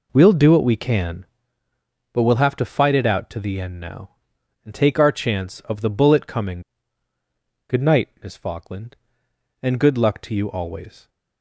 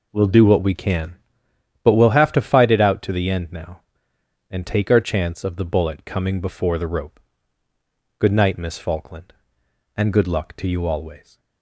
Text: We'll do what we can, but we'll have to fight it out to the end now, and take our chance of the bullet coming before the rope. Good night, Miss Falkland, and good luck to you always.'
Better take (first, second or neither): second